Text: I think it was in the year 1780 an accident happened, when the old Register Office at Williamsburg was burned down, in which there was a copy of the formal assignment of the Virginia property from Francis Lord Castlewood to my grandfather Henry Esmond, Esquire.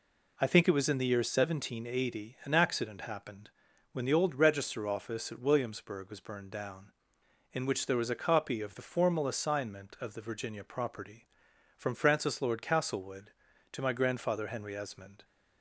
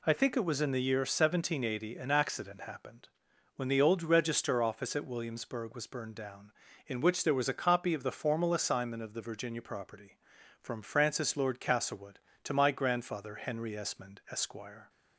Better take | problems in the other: second | stops before "Esquire"; at 15.2 s

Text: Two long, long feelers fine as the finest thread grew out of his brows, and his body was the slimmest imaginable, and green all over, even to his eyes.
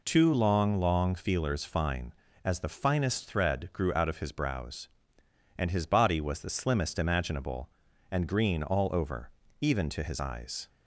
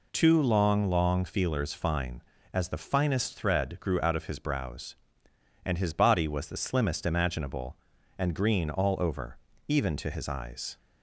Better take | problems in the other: neither | none

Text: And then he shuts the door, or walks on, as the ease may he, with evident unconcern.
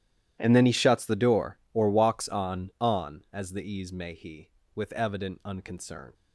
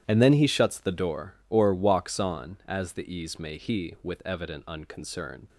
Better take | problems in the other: second | starts louder than the rest; strong; until 1.4 s; 12.5 dB; strong in the second // says "on" twice; at 2.7 s

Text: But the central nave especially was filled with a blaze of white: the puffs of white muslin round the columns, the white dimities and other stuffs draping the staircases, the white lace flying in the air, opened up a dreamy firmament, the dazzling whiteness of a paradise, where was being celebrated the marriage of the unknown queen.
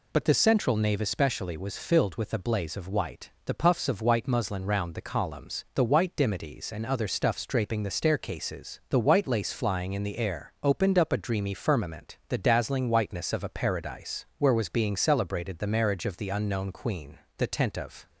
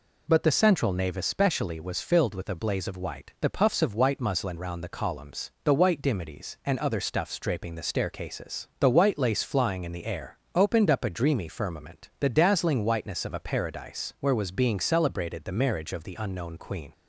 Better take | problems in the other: second | goes on to say "The tent of"; noticeable; from 17.3 s on; 0.72 s long

